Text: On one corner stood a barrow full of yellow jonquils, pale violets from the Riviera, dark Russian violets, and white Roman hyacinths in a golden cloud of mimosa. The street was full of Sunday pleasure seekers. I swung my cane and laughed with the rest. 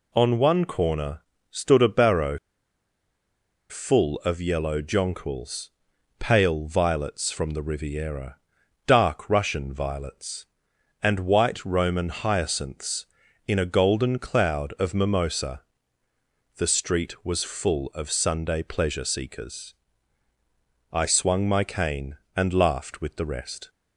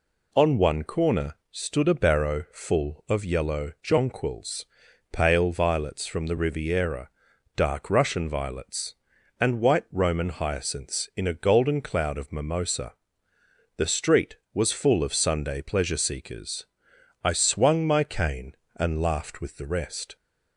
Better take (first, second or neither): second